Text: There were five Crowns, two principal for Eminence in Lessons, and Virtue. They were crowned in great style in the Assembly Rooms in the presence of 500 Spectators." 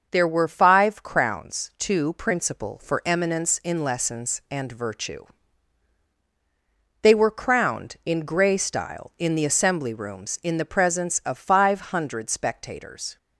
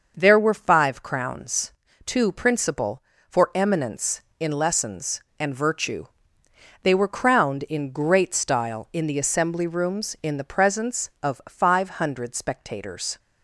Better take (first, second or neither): second